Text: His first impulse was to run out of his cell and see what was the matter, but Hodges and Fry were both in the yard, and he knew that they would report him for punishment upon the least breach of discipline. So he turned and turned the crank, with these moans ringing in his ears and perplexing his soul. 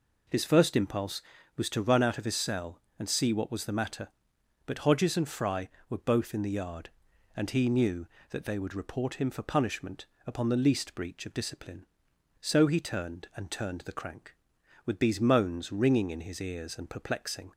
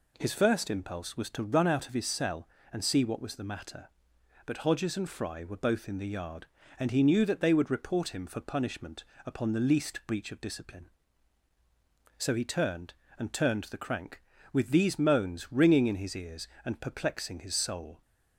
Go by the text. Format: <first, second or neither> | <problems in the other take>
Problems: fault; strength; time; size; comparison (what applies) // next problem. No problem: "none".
second | pauses between "punishment" and "upon"; slight; at 10.0 s; 0.20 s long; slight in the second // stops before "his soul"; at 17.5 s